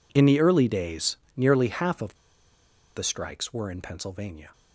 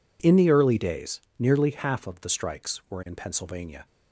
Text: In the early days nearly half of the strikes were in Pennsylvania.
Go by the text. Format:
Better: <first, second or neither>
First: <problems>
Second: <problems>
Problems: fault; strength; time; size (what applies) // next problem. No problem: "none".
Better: second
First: pauses between "days" and "nearly"; slight; at 1.1 s; 0.22 s long // pauses between "of" and "the"; noticeable; at 2.1 s; 0.81 s long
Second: pauses between "days" and "nearly"; slight; at 1.1 s; 0.20 s long